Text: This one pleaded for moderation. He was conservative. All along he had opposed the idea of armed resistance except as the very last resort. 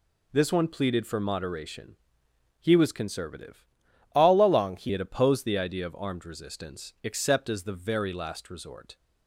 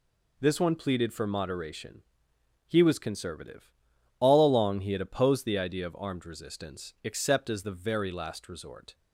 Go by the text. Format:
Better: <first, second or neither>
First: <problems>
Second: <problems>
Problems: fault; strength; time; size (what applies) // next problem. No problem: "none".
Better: second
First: changes voice from "All" to "he"; from 4.1 to 4.8 s; 0.7 s long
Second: none